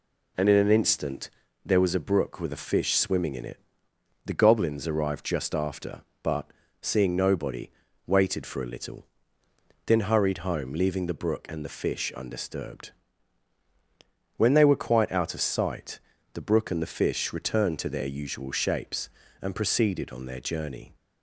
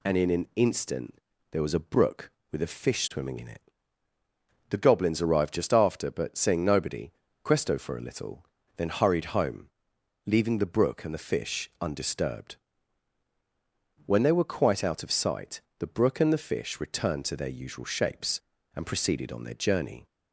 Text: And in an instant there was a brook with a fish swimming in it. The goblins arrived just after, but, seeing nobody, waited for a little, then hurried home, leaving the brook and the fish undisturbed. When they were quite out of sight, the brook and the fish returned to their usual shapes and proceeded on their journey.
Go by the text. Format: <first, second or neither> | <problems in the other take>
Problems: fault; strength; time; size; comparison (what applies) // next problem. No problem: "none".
first | pauses between "instant" and "there"; slight; at 1.1 s; 0.36 s long; slight in the first // says "questo" for "waited"; at 7.4 s